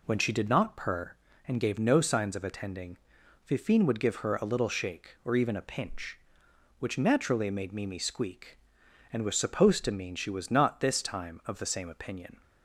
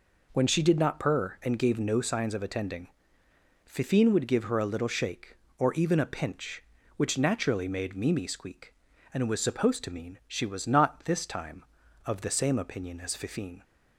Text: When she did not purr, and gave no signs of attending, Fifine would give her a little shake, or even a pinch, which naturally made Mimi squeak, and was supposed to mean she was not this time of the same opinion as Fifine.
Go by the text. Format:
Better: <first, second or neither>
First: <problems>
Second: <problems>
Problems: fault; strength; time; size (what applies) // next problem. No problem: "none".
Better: second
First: stops before "as Fifine"; at 12.4 s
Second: none